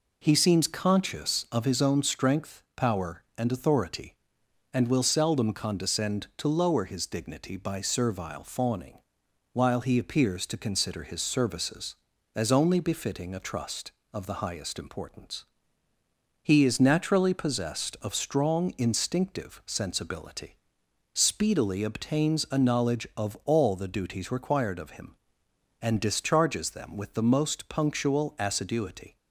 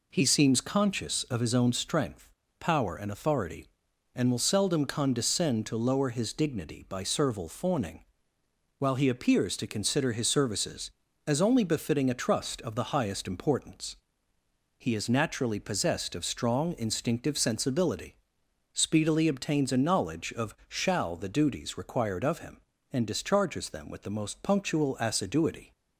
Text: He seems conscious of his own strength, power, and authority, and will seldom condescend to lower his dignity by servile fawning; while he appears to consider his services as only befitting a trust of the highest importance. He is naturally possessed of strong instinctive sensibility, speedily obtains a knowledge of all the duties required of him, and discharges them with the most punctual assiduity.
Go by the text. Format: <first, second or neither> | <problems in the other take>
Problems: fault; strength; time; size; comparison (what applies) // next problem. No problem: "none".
first | says "shall" for "all"; at 20.6 s